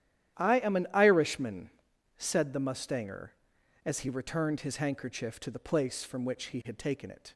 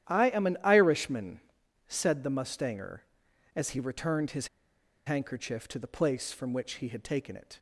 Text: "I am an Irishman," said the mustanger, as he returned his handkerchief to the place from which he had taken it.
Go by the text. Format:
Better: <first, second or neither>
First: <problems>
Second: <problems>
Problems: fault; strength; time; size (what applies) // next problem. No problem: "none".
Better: first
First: starts louder than the rest; strong; until 1.4 s; 11 dB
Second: starts louder than the rest; strong; until 1.1 s; 11 dB // pauses between "his" and "handkerchief"; noticeable; at 4.4 s; 0.57 s long